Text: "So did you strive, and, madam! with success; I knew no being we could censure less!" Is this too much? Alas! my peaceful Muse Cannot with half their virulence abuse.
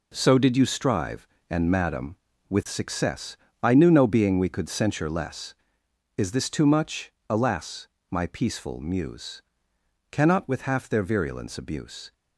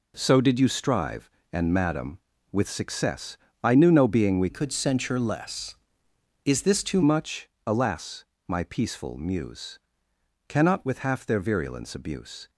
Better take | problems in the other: first | changes voice from "could" to "too"; from 4.4 to 7.0 s; 2.6 s long // pauses between "Muse" and "Cannot"; noticeable; at 9.7 s; 0.70 s long; noticeable in the first

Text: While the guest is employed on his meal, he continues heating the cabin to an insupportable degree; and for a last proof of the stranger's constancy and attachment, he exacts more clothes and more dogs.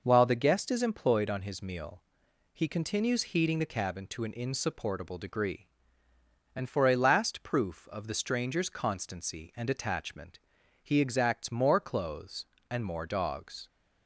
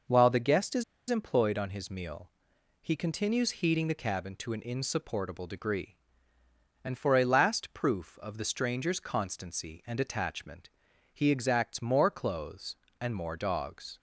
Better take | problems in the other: first | pauses between "is" and "employed"; slight; at 0.8 s; 0.26 s long

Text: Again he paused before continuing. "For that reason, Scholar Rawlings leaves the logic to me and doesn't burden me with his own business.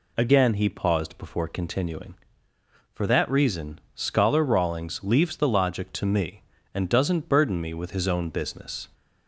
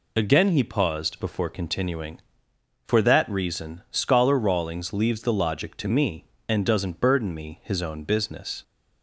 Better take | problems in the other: first | skips "with"; at 7.6 s

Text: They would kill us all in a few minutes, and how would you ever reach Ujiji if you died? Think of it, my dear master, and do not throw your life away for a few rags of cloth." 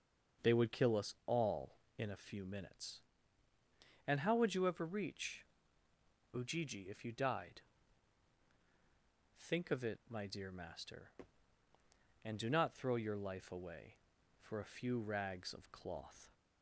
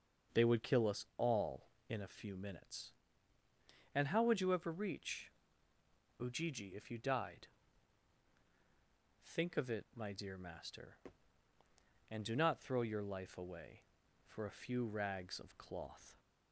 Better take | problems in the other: neither | starts louder than the rest; the same in both // pauses between "reach" and "Ujiji"; noticeable; the same in both

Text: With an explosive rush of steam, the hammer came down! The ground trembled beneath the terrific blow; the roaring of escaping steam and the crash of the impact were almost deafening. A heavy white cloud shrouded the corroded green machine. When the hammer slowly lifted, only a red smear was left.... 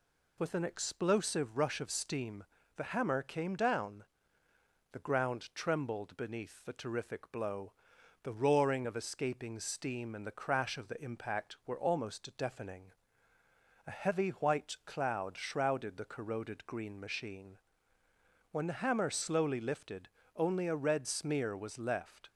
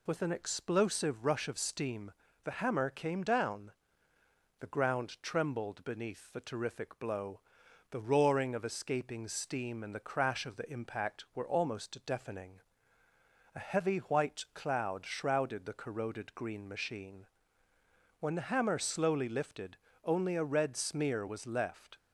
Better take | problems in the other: neither | none

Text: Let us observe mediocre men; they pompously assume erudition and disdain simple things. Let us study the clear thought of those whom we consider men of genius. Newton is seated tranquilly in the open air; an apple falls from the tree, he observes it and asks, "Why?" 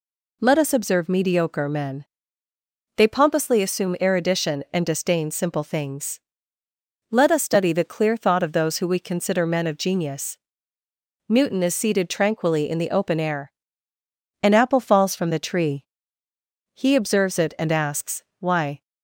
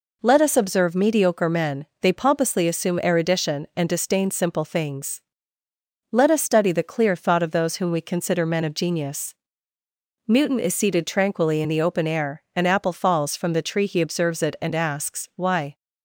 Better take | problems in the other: second | says "who" for "whom"; at 8.7 s

